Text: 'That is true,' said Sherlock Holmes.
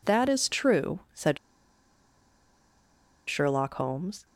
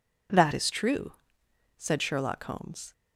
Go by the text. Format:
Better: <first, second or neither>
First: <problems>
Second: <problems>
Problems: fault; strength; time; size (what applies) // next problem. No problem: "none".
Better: second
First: pauses between "said" and "Sherlock"; strong; at 1.3 s; 1.9 s long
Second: none